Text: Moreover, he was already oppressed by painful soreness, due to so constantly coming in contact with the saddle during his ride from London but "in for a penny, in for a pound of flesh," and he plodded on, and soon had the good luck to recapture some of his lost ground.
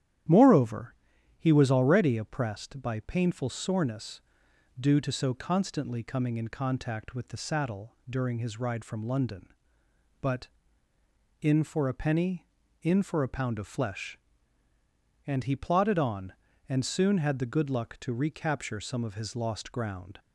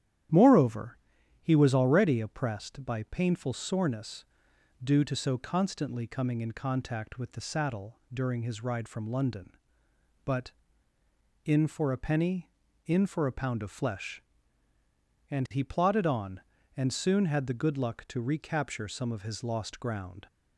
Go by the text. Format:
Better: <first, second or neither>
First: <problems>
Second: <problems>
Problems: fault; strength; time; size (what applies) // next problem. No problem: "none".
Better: neither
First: starts louder than the rest; strong; until 1.7 s; 11 dB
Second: starts louder than the rest; strong; until 1.7 s; 11 dB